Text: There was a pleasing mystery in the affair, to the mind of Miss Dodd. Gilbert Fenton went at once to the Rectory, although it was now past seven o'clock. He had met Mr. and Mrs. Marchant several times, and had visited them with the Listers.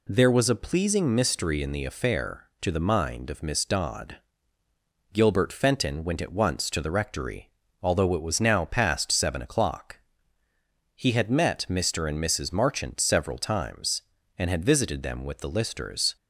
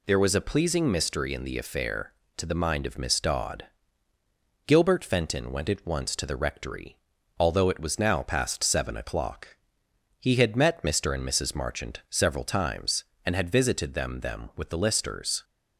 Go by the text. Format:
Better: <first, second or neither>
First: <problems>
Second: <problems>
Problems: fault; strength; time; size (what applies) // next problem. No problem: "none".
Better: first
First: none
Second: says "them" twice; at 14.2 s